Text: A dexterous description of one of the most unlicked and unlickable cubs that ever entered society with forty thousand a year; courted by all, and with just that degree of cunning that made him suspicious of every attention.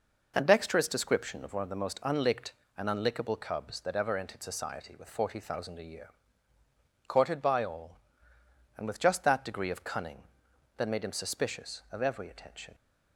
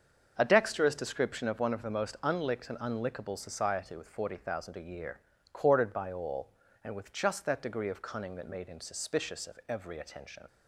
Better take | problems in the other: first | starts louder than the rest; until 1.3 s; 6.5 dB // skips "cubs that ever entered"; at 3.3 s

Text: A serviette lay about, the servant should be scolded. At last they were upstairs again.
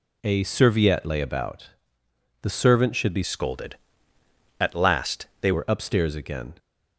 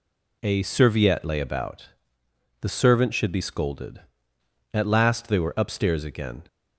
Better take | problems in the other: second | changes voice from "scolded" to "they"; from 3.2 to 5.5 s; 2.3 s long // pauses between "last" and "they"; slight; at 5.2 s; 0.16 s long

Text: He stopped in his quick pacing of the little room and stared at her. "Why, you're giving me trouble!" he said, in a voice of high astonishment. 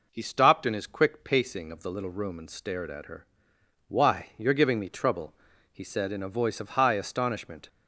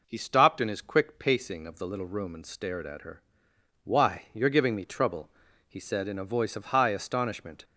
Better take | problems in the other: neither | none

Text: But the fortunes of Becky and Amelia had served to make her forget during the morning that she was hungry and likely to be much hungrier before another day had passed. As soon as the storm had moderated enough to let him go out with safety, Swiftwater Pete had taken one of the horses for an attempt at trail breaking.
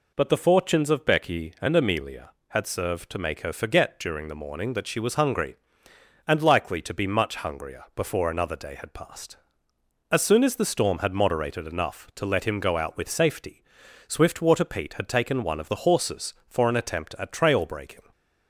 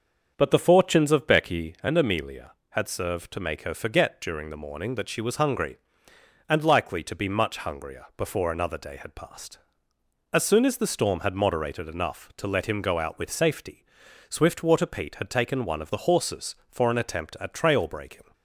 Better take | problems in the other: first | starts louder than the rest; until 1.8 s; 7 dB

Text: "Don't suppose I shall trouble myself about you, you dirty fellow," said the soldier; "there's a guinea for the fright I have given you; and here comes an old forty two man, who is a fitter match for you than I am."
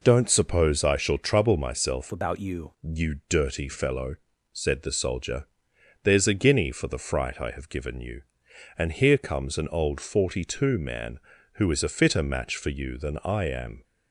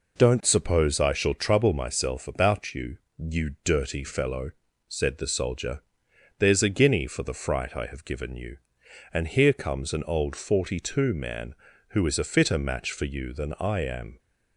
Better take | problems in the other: second | changes voice from "about" to "you"; from 2.1 to 2.7 s; 0.6 s long

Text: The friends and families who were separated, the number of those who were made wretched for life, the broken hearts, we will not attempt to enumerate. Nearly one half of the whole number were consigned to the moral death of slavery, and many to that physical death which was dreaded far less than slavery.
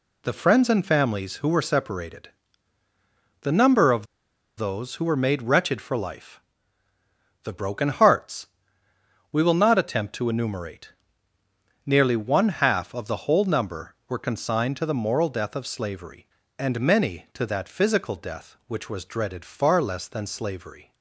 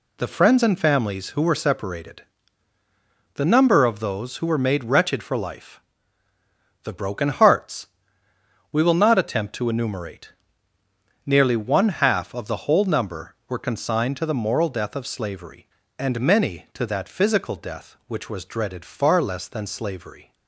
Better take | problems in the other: second | pauses between "of" and "those"; noticeable; at 4.0 s; 0.51 s long

